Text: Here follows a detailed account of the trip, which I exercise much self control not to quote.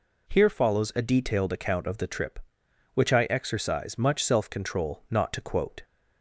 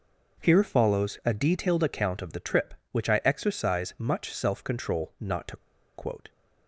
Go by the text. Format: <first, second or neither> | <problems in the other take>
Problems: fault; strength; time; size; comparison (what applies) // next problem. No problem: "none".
first | pauses between "to" and "quote"; at 5.5 s; 0.39 s long